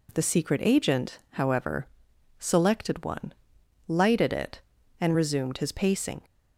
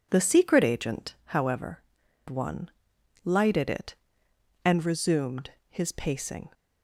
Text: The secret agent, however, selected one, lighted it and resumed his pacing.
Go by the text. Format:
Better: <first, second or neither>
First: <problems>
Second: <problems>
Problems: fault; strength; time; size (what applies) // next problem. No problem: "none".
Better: first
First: none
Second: skips "selected"; at 2.0 s // pauses between "resumed" and "his"; slight; at 5.5 s; 0.18 s long